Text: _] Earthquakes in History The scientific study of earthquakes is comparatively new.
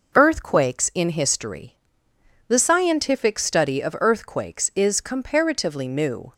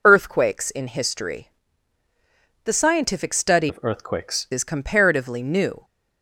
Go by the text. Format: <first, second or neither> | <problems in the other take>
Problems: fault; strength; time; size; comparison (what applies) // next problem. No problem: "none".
first | pauses between "History" and "The"; at 1.4 s; 1.1 s long; noticeable in the first // changes voice from "of" to "earthquakes"; from 3.6 to 4.4 s; 0.8 s long